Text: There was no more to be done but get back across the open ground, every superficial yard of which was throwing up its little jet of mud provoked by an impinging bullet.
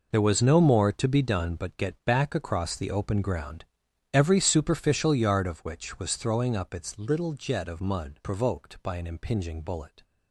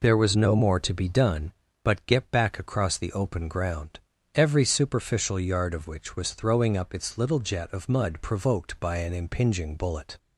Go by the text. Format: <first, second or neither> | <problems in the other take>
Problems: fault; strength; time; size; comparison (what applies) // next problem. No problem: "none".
second | gets quieter; strong; throughout; 12.5 dB